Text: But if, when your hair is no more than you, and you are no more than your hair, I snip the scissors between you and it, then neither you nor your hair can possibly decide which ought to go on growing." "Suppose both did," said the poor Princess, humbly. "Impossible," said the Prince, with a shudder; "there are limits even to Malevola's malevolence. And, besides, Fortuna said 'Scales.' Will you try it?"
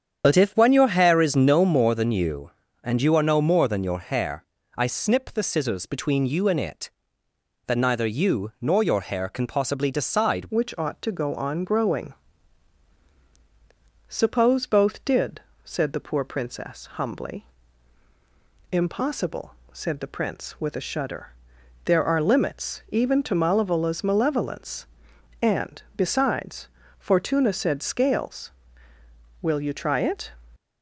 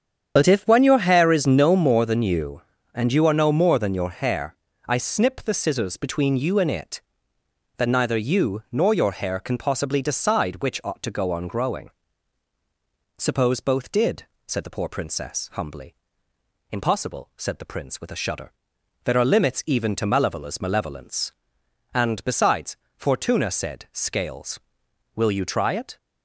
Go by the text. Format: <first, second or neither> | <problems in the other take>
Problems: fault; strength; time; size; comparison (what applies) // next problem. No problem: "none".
second | starts louder than the rest; strong; until 1.2 s; 8 dB; strong in the second // changes voice at "which"; from 10.4 s on; 19.9 s long